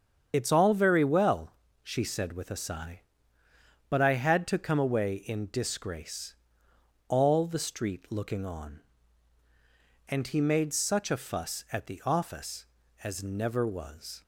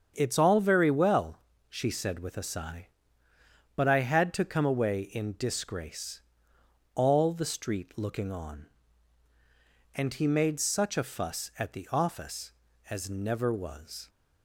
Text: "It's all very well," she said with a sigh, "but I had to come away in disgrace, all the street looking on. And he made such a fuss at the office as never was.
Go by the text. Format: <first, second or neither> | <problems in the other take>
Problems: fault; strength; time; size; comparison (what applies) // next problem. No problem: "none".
second | loses the start of "It's"; at 0.3 s; 60 ms // starts louder than the rest; strong; until 1.3 s; 7.5 dB; strong in the second